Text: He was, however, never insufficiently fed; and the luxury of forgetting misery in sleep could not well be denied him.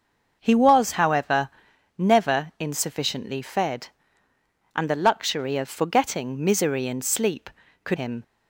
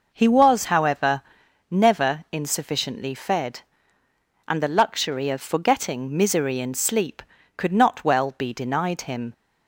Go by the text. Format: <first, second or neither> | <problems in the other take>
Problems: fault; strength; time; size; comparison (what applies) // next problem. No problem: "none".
second | starts louder than the rest; until 1.4 s; 6 dB // skips "not well be denied"; at 7.9 s